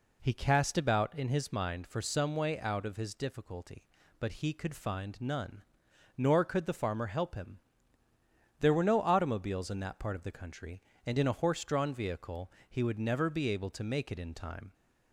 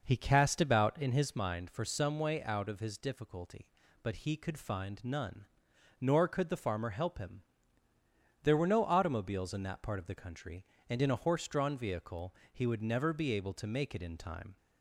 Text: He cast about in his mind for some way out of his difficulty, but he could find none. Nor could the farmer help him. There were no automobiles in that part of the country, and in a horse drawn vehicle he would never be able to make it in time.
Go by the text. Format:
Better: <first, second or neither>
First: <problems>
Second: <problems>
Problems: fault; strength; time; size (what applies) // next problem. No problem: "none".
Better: first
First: pauses between "vehicle" and "he"; slight; at 12.5 s; 0.18 s long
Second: starts louder than the rest; noticeable; until 1.4 s; 5.5 dB // pauses between "vehicle" and "he"; slight; at 12.3 s; 0.18 s long